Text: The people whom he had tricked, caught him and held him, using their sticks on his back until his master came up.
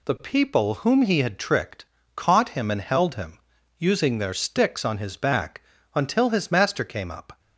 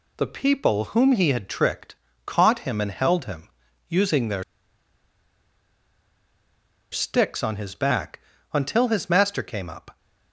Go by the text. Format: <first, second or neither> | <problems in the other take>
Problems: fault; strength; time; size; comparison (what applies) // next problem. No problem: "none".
first | pauses between "their" and "sticks"; strong; at 4.4 s; 2.4 s long // pauses between "back" and "until"; slight; at 8.1 s; 0.34 s long; slight in the first